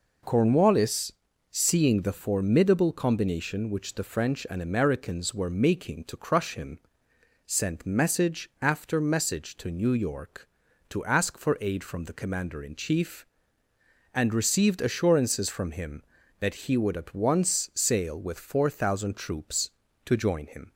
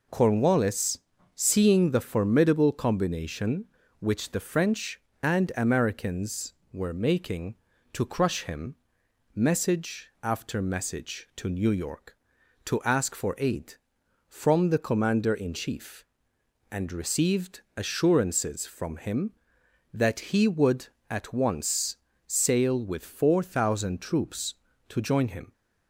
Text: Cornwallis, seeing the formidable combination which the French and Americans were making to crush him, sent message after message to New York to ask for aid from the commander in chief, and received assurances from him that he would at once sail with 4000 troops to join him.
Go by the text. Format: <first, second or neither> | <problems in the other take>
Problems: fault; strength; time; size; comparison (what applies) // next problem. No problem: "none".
first | skips "sent"; at 9.0 s // pauses between "received" and "assurances"; slight; at 17.6 s; 0.16 s long // pauses between "once" and "sail"; slight; at 21.9 s; 0.30 s long